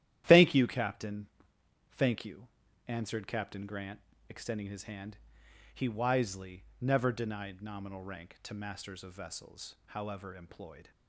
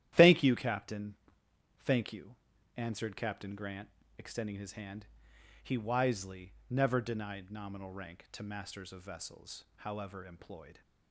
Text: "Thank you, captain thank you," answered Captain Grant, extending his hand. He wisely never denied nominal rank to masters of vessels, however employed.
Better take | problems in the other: neither | starts louder than the rest; strong; the same in both // pauses between "captain" and "thank"; noticeable; the same in both // pauses between "wisely" and "never"; slight; the same in both

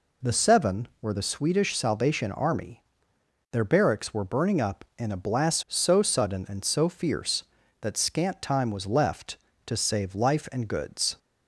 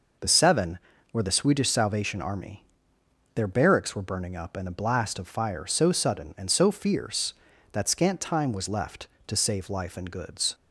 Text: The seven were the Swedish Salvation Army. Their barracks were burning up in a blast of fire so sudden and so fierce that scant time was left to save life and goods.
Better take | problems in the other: second | skips "of fire"; at 5.6 s

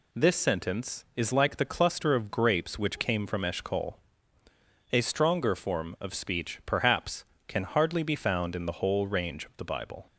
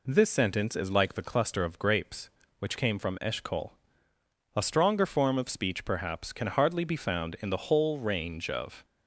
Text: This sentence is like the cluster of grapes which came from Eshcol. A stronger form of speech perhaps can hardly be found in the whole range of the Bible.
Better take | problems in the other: first | stops before "the Bible"; at 8.8 s

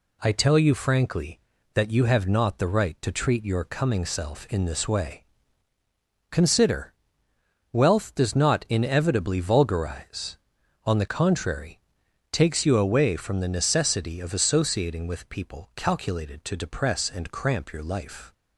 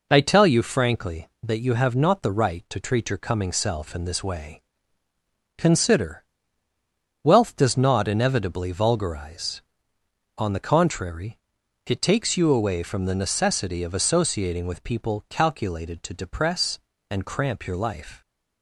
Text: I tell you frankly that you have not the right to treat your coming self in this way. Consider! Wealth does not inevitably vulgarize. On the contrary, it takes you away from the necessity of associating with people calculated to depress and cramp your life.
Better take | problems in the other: second | skips "it"; at 12.0 s

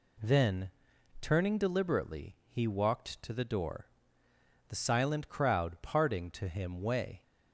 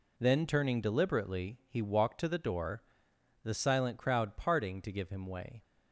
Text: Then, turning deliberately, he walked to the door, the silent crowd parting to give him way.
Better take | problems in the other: second | skips "give"; at 6.4 s

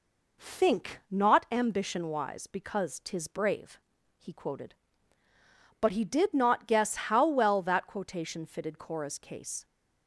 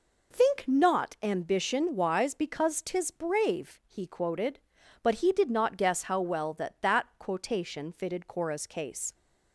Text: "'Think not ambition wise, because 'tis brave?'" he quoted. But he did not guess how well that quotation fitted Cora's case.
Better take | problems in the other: first | says "that" twice; at 6.7 s

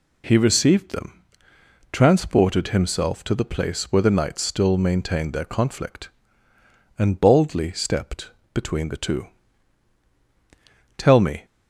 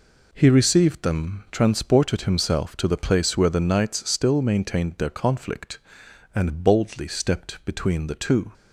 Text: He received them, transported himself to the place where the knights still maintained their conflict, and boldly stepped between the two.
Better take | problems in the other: second | pauses between "stepped" and "between"; slight; at 8.3 s; 0.24 s long // goes on to say "Tell me"; slight; from 10.9 s on; 0.48 s long

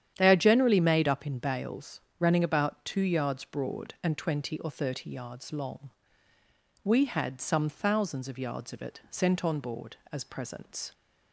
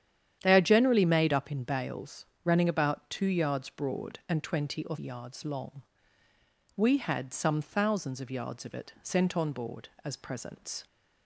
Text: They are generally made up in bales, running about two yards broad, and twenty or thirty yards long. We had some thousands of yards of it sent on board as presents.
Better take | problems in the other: first | starts louder than the rest; strong; until 1.4 s; 10 dB; strong in the first // skips "thirty"; at 4.9 s

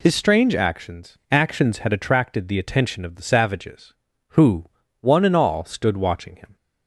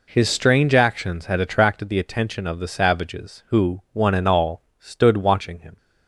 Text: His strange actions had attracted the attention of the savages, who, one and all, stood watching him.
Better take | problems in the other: second | says "actions" twice; at 1.2 s

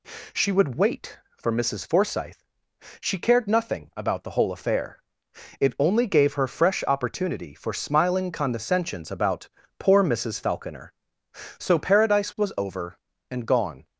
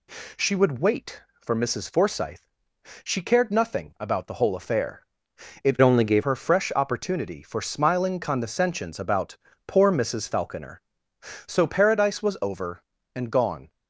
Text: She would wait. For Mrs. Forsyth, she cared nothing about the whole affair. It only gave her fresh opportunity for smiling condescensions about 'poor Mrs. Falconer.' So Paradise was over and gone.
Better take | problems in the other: first | changes voice from "only" to "gave"; from 5.8 to 6.2 s; 0.4 s long // pauses between "about" and "poor"; slight; at 9.3 s; 0.32 s long; slight in the first

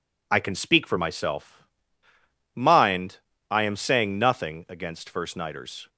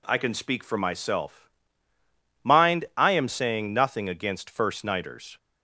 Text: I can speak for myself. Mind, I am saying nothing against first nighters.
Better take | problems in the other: neither | none

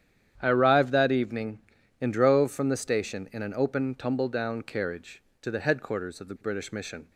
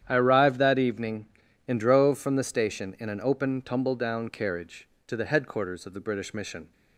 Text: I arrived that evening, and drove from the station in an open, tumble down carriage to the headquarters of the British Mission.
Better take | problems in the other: neither | starts louder than the rest; strong; the same in both

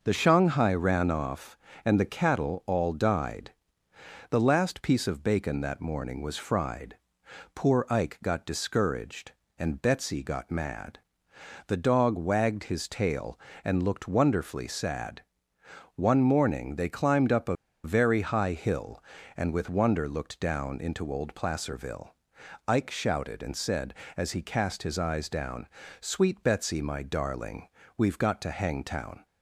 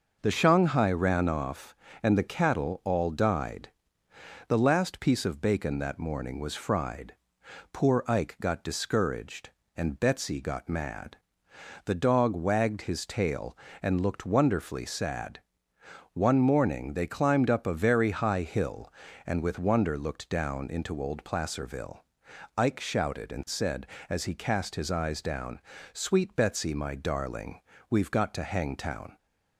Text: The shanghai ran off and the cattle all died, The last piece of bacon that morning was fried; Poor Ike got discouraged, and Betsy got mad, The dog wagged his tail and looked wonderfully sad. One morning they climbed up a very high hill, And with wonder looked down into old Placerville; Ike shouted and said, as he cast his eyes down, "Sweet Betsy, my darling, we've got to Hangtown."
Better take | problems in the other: second | pauses between "a" and "very"; slight; at 17.5 s; 0.29 s long

